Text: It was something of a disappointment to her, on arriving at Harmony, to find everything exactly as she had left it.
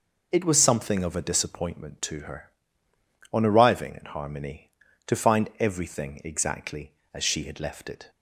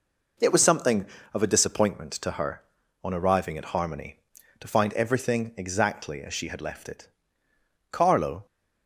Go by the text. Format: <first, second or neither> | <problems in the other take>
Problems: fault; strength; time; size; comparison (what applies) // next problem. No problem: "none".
first | goes on to say "Carlo"; from 7.9 s on; 0.54 s long